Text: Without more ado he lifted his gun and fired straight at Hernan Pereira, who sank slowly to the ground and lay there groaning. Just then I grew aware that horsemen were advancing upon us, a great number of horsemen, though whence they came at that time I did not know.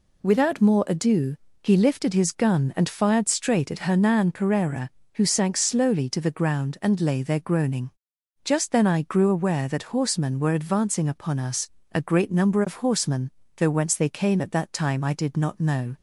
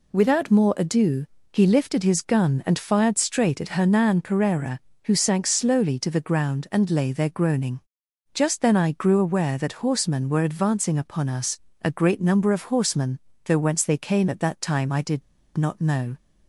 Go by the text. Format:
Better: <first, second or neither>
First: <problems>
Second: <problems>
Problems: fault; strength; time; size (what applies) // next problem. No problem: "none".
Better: first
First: pauses between "ado" and "he"; slight; at 1.3 s; 0.26 s long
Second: pauses between "ado" and "he"; slight; at 1.2 s; 0.26 s long // pauses between "did" and "not"; slight; at 15.2 s; 0.34 s long